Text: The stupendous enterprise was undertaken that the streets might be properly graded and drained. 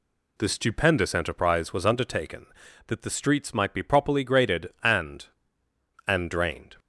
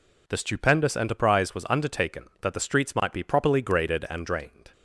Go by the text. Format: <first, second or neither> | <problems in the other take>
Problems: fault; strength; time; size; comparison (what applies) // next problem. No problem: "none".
second | says "and" twice; at 6.0 s